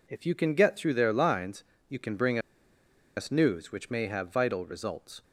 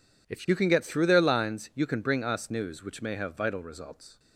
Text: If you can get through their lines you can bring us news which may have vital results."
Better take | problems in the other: second | pauses between "lines" and "you"; slight; at 1.6 s; 0.26 s long // pauses between "bring" and "us"; noticeable; at 2.3 s; 0.78 s long

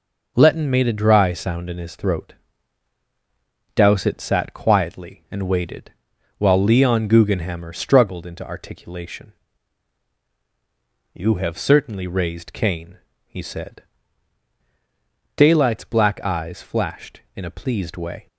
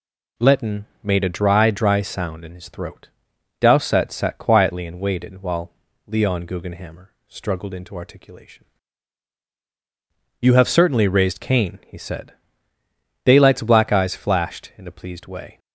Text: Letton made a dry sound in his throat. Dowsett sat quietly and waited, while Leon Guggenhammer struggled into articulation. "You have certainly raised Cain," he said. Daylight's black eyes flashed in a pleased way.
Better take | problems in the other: first | pauses between "Letton" and "made"; slight; at 0.8 s; 0.18 s long // says "dry" twice; at 1.7 s // pauses between "while" and "Leon"; slight; at 5.7 s; 0.36 s long // pauses between "Guggenhammer" and "struggled"; slight; at 7.0 s; 0.18 s long

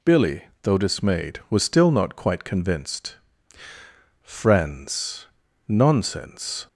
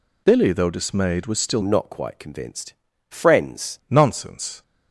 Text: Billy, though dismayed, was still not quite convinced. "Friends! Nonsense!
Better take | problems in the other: first | changes voice from "not" to "Friends"; from 1.6 to 3.7 s; 2.1 s long

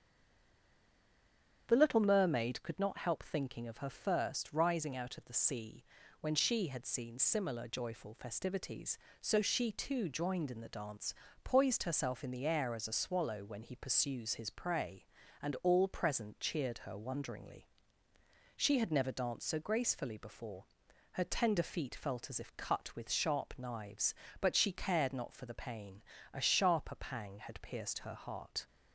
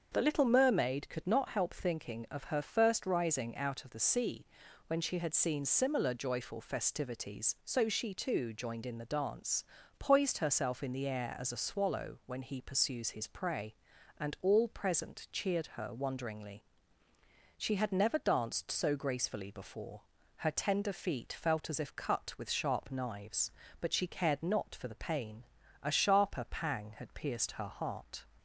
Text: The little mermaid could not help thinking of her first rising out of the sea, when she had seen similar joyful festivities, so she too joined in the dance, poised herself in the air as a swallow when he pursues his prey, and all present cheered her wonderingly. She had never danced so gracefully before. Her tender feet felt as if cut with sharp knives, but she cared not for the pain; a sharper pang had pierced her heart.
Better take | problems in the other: second | stays silent before the first word; noticeable; until 1.6 s; 1.6 s long // starts louder than the rest; strong; until 2.6 s; 8.5 dB; also in the second

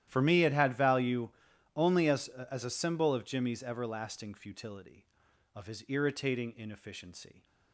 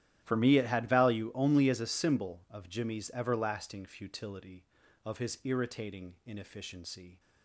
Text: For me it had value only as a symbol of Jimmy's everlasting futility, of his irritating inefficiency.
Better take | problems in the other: second | starts louder than the rest; strong; until 1.0 s; 12 dB; strong in the second // pauses between "value" and "only"; noticeable; at 1.2 s; 0.48 s long // says "as" twice; at 2.2 s

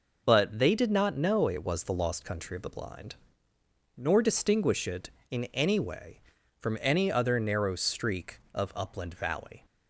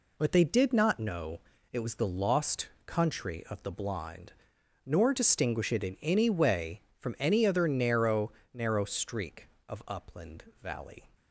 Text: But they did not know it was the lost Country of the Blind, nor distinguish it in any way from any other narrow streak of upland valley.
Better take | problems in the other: first | pauses between "know" and "it"; slight; at 1.4 s; 0.32 s long // pauses between "lost" and "Country"; slight; at 2.6 s; 0.18 s long // says "narrow" twice; at 8.5 s // pauses between "upland" and "valley"; slight; at 10.4 s; 0.18 s long

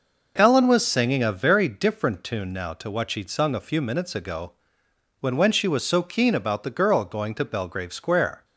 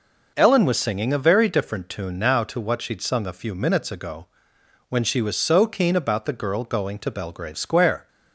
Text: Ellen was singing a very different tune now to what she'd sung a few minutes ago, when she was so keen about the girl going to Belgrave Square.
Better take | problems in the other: second | says "when" twice; at 5.3 s

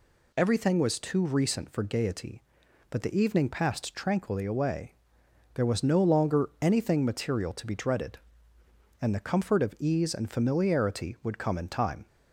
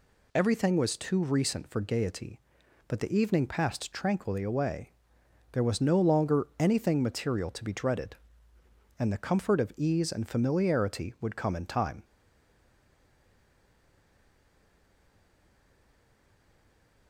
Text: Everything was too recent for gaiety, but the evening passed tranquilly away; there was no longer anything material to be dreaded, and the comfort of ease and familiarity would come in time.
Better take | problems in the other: first | stays silent after the last word; strong; from 12.0 s on; 5.0 s long

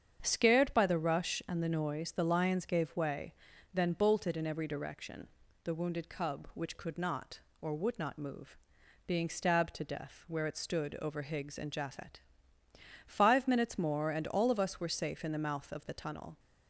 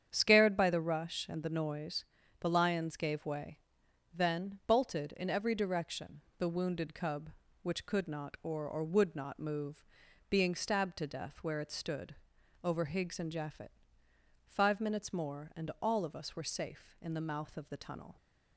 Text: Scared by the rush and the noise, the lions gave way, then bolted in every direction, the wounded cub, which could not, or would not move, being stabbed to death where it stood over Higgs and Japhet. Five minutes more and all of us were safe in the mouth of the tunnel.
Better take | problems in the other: first | starts louder than the rest; strong; until 1.1 s; 8.5 dB; strong in the first // says "or" twice; at 8.6 s // pauses between "stood" and "over"; noticeable; at 12.1 s; 0.48 s long

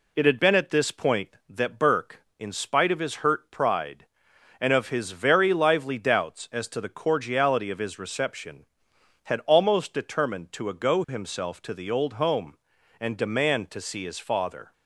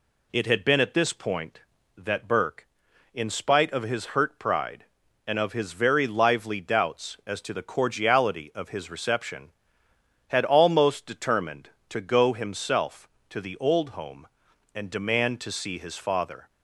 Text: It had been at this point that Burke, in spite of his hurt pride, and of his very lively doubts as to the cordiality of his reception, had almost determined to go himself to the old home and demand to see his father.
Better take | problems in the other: second | says "ago" for "go"; at 10.6 s

